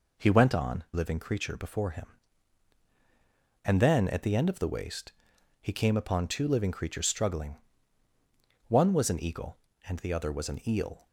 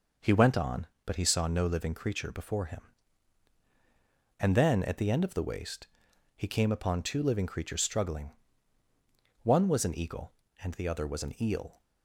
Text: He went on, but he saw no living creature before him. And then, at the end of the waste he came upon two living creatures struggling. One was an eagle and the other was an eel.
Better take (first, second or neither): second